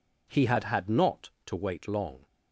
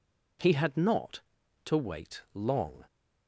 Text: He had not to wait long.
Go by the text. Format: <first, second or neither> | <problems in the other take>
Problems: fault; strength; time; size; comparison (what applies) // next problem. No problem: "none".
second | says "had" twice; at 0.6 s